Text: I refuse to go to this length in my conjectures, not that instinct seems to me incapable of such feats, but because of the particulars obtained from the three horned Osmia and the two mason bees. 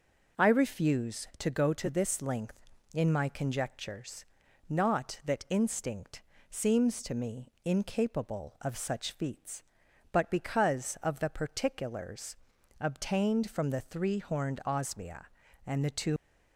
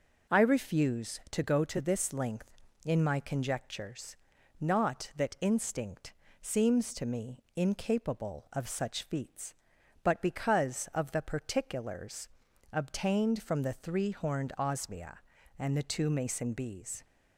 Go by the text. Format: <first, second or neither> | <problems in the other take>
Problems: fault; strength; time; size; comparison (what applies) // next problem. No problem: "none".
second | pauses between "instinct" and "seems"; slight; at 6.2 s; 0.28 s long; slight in the second // pauses between "particulars" and "obtained"; noticeable; at 12.3 s; 0.46 s long; noticeable in the second // stops before "mason bees"; at 16.1 s